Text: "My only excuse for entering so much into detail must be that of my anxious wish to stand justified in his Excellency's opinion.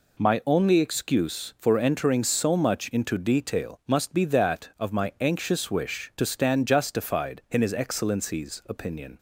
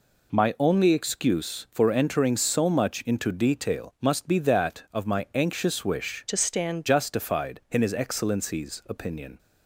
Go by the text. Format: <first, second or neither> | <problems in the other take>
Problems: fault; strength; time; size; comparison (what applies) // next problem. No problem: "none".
first | changes voice from "to" to "stand"; from 6.2 to 6.8 s; 0.6 s long